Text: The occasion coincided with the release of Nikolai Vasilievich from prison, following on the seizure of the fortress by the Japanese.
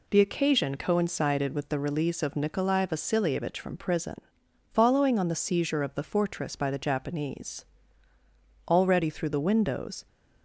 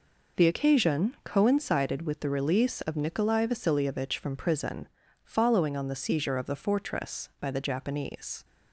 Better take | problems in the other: second | goes on to say "Already through the windows"; from 8.6 s on; 1.3 s long

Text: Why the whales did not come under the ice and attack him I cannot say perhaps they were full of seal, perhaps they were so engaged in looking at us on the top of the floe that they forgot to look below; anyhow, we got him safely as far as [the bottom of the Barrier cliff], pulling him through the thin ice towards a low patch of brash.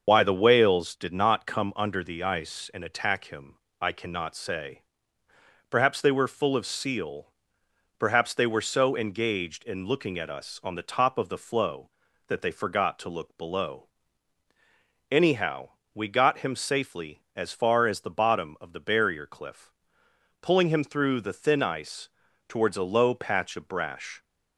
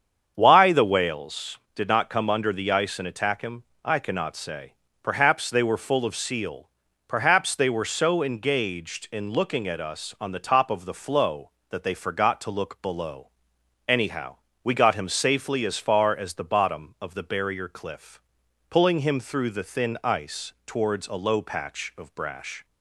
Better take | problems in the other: second | loses the start of "Why"; at 0.0 s; 45 ms // starts louder than the rest; until 1.0 s; 6.5 dB; strong in the second // pauses between "him" and "I"; slight; at 3.5 s; 0.24 s long; slight in the second // pauses between "say" and "perhaps"; noticeable; at 4.8 s; 0.88 s long; slight in the second // pauses between "ice" and "towards"; at 22.0 s; 0.38 s long; slight in the second

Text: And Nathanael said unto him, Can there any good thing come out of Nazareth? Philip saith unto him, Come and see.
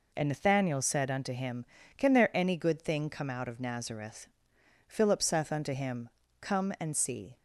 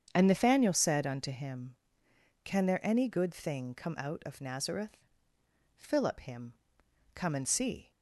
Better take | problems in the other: first | starts louder than the rest; strong; until 1.1 s; 7.5 dB // skips "saith unto"; at 6.1 s

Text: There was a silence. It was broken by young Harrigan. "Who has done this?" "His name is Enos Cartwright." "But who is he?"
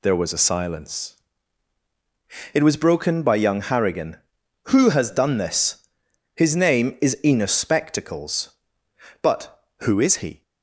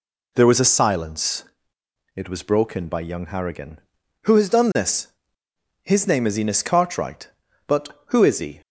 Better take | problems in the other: second | says "Spectacles" for "Cartwright"; at 7.5 s

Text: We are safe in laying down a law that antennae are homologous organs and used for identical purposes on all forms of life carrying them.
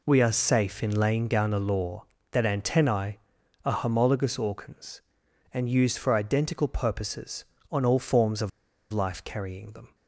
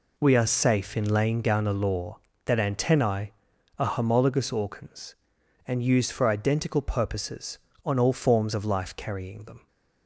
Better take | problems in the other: second | pauses between "of" and "life"; at 8.4 s; 0.40 s long

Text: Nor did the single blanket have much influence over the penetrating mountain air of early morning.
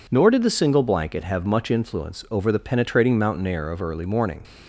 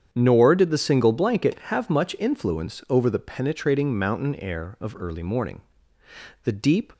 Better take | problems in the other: first | starts louder than the rest; strong; until 1.1 s; 8.5 dB // goes on to say "The deep"; slight; from 6.4 s on; 0.48 s long

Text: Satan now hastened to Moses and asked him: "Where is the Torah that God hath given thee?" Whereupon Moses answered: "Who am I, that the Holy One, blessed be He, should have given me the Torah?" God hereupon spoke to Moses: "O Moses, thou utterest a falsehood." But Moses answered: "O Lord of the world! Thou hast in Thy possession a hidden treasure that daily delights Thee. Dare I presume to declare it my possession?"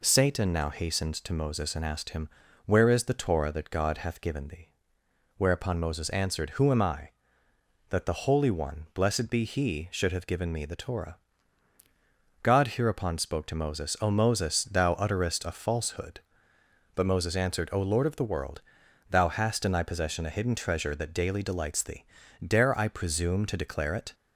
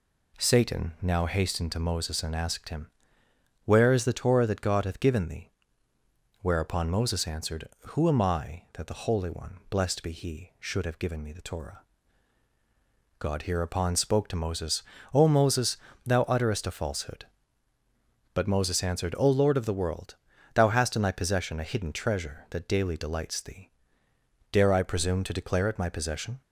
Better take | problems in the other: second | stops before "my possession"; at 24.1 s

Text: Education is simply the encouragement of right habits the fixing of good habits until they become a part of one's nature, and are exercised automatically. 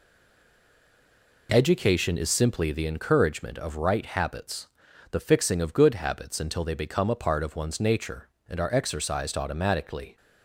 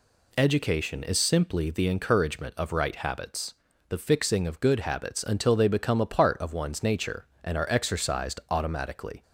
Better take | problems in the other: second | stays silent before the first word; noticeable; until 1.4 s; 1.4 s long // pauses between "habits" and "the"; at 4.6 s; 0.42 s long; slight in the second

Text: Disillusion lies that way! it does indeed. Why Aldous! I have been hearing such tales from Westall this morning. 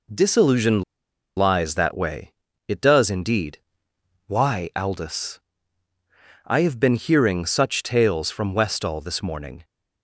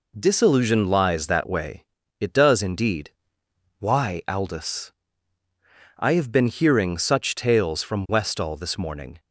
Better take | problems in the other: second | pauses between "Disillusion" and "lies"; noticeable; at 0.8 s; 0.55 s long

